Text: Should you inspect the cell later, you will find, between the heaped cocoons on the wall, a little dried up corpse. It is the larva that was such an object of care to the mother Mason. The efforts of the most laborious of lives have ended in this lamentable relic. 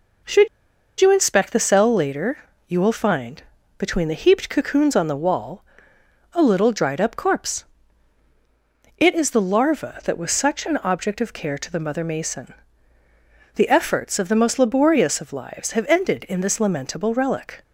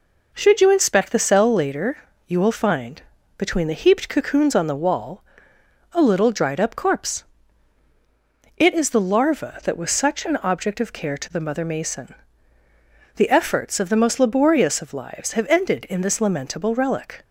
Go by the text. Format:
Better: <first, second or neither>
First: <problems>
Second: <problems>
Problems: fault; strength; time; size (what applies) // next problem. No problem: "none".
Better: second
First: pauses between "Should" and "you"; noticeable; at 0.4 s; 0.52 s long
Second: none